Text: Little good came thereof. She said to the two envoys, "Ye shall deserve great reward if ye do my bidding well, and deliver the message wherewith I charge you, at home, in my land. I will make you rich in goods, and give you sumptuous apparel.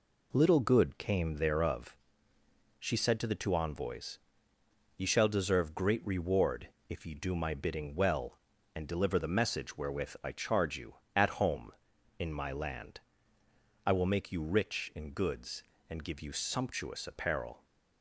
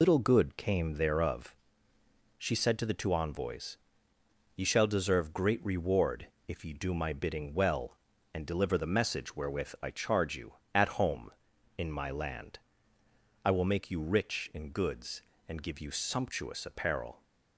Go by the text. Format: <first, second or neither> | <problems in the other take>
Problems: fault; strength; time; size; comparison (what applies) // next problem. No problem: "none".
first | loses the start of "Little"; at 0.0 s; 100 ms // pauses between "reward" and "if"; slight; at 6.2 s; 0.20 s long; slight in the first